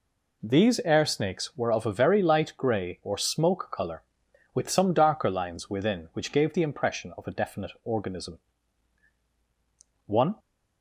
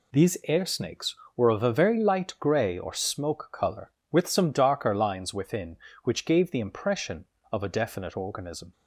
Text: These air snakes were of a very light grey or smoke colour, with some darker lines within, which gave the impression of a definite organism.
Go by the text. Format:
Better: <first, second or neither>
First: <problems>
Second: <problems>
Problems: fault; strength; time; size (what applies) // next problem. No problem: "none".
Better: second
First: goes on to say "One"; slight; from 10.0 s on; 0.30 s long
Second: none